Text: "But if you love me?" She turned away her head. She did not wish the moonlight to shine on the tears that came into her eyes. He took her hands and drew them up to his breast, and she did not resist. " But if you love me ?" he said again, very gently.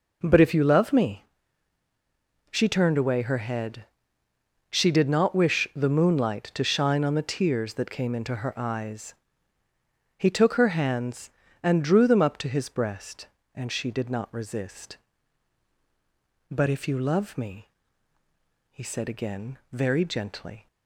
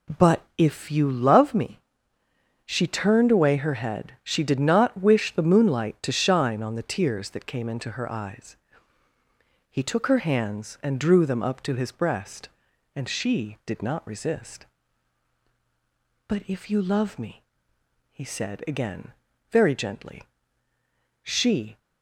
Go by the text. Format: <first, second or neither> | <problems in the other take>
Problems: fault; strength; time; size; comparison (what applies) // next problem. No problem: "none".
first | pauses between "But" and "if"; slight; at 0.4 s; 0.16 s long // goes on to say "She"; from 21.2 s on; 0.54 s long